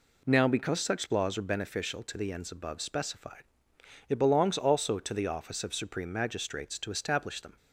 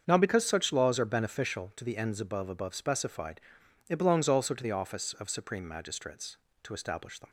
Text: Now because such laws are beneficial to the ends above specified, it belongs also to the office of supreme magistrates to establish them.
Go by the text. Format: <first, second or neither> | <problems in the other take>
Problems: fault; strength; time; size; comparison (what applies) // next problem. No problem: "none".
first | starts louder than the rest; until 1.0 s; 7 dB // says "above" twice; at 2.4 s